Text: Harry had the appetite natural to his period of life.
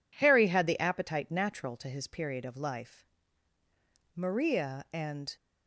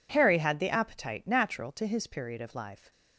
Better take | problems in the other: second | goes on to say "Maria and"; noticeable; from 4.1 s on; 1.2 s long

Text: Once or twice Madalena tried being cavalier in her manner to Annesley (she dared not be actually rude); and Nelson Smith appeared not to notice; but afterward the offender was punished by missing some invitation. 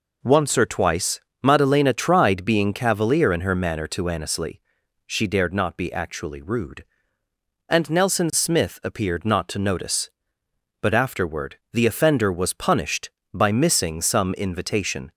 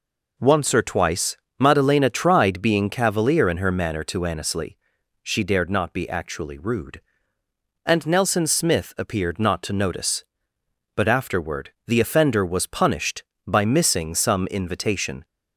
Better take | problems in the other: neither | pauses between "twice" and "Madalena"; slight; the same in both // pauses between "afterward" and "the"; slight; the same in both

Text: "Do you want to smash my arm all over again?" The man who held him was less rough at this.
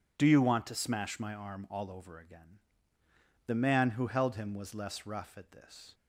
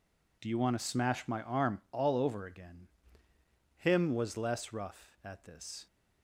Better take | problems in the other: first | skips "The man who held"; at 3.3 s

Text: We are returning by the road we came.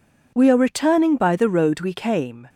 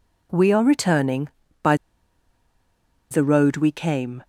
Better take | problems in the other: first | pauses between "by" and "the"; strong; at 1.7 s; 1.3 s long

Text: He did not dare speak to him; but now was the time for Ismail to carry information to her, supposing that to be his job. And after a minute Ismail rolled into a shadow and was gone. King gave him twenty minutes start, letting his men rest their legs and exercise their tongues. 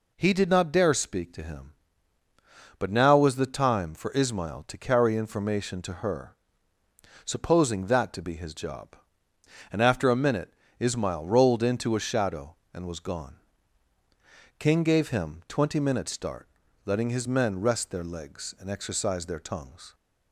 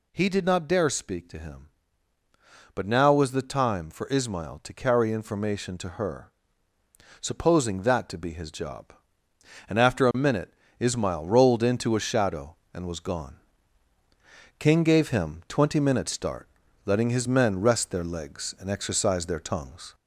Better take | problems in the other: first | gets louder; slight; throughout; 2.5 dB // pauses between "minute" and "Ismail"; slight; at 10.5 s; 0.26 s long; slight in the first

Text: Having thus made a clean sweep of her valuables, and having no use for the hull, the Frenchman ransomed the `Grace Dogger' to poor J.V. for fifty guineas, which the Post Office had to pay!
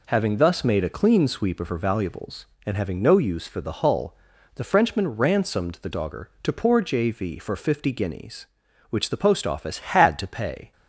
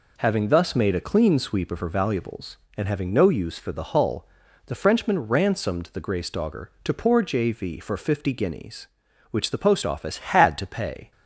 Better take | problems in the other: second | skips "Grace"; at 5.9 s

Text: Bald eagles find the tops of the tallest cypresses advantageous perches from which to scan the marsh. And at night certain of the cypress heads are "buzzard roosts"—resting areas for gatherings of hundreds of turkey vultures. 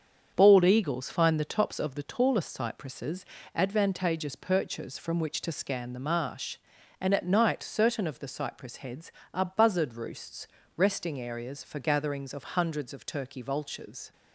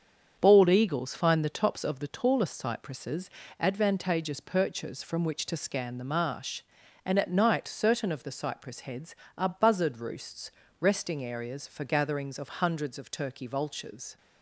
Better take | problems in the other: neither | starts louder than the rest; strong; the same in both // pauses between "cypresses" and "advantageous"; slight; the same in both

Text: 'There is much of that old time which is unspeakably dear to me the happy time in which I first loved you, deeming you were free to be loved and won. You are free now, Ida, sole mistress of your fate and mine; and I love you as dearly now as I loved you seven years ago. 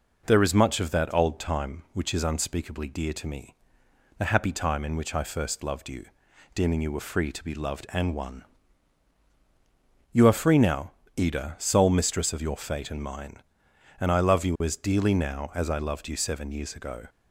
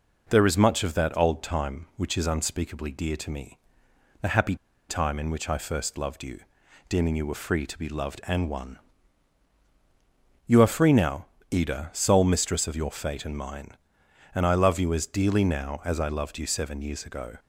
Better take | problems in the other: first | pauses between "me" and "the"; noticeable; at 3.5 s; 0.64 s long; noticeable in the first // pauses between "happy" and "time"; slight; at 4.5 s; 0.33 s long

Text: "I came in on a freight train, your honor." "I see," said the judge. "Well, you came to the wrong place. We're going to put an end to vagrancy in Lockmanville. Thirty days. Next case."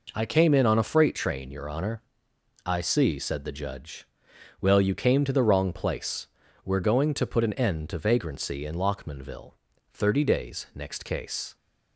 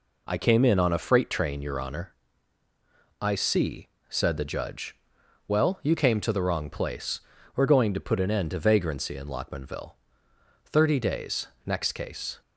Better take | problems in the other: neither | none

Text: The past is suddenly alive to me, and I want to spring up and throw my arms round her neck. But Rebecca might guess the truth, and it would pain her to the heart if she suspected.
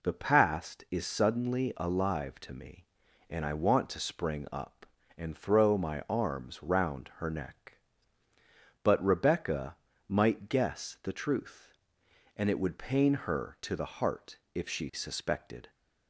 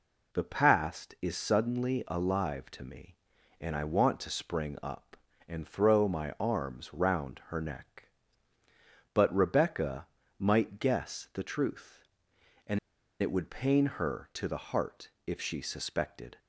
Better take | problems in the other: first | pauses between "Rebecca" and "might"; slight; at 10.0 s; 0.32 s long; slight in the first // pauses between "and" and "it"; at 12.7 s; 0.41 s long // pauses between "heart" and "if"; slight; at 15.1 s; 0.16 s long; slight in the first

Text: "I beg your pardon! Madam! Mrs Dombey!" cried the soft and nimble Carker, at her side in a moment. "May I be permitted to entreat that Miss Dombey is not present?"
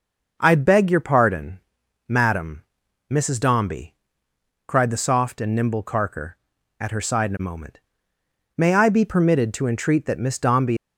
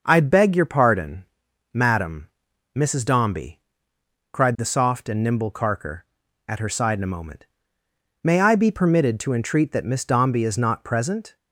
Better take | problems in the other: second | stops before "is not present"; at 10.7 s

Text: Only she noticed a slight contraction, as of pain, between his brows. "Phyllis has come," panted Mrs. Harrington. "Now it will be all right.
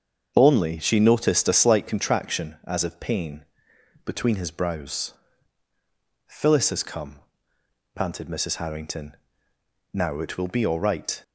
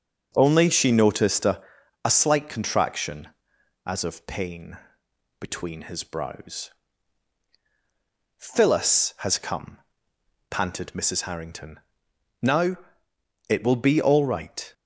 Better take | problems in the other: first | starts louder than the rest; noticeable; until 1.3 s; 6 dB; also in the first // says "a" twice; at 2.0 s // pauses between "Now" and "it"; noticeable; at 12.7 s; 0.70 s long

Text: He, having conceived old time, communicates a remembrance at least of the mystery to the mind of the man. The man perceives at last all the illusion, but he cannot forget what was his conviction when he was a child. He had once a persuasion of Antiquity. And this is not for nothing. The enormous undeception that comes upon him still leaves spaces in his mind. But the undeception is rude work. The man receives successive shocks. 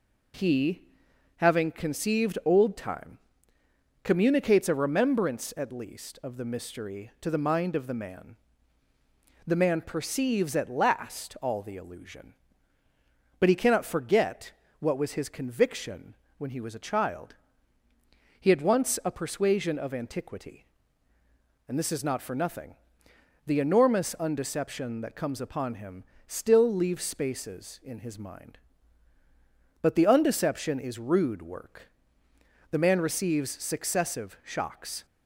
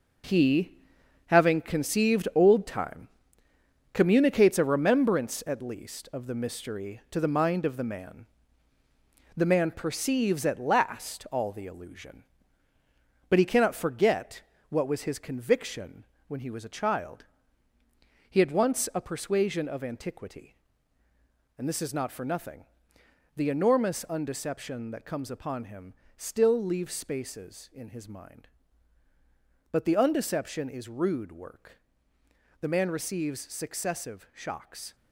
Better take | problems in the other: first | gets quieter; strong; throughout; 9 dB // pauses between "forget" and "what"; slight; at 14.4 s; 0.30 s long; slight in the first // pauses between "conviction" and "when"; slight; at 16.0 s; 0.20 s long; slight in the first // pauses between "him" and "still"; slight; at 25.9 s; 0.24 s long; slight in the first

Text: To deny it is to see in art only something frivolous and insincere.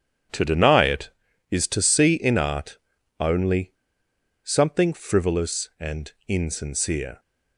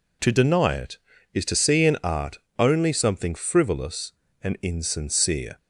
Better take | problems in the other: second | starts louder than the rest; strong; until 1.7 s; 9 dB // pauses between "art" and "only"; at 2.7 s; 0.42 s long; slight in the second // pauses between "only" and "something"; noticeable; at 3.7 s; 0.72 s long // pauses between "and" and "insincere"; slight; at 6.1 s; 0.16 s long

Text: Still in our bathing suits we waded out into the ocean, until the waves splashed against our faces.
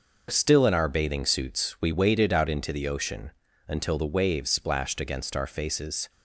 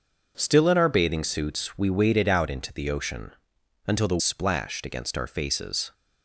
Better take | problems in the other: first | skips "waves"; at 4.1 s

